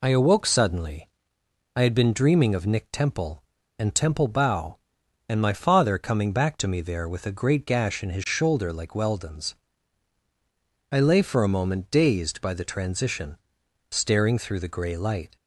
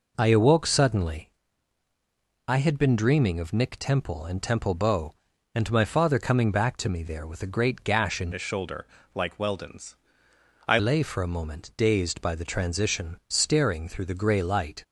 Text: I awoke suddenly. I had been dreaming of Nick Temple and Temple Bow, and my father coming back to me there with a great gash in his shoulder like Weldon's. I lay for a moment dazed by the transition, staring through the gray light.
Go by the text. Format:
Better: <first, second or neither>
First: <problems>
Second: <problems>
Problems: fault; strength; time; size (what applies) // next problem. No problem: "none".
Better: first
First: none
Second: changes voice from "his" to "I"; from 8.3 to 10.7 s; 2.4 s long // pauses between "shoulder" and "like"; slight; at 8.8 s; 0.30 s long